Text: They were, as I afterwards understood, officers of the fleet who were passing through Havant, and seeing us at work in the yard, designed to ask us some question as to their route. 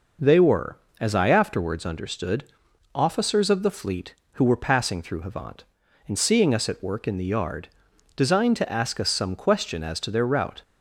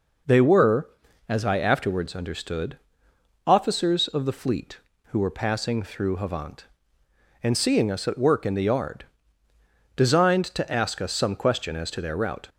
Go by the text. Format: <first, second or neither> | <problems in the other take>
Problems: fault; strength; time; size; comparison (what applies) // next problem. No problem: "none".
neither | none